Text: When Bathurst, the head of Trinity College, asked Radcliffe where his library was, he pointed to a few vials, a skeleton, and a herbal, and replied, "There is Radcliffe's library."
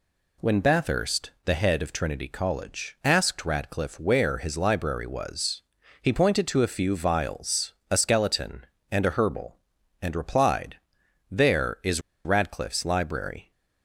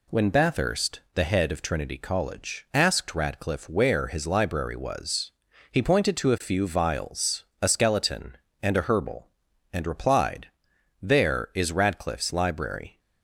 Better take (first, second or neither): second